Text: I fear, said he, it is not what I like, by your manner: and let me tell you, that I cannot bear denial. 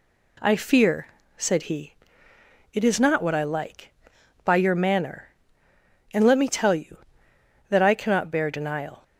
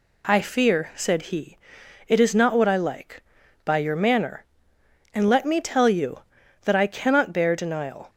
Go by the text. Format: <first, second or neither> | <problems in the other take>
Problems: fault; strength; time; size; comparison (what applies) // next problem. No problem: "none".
neither | none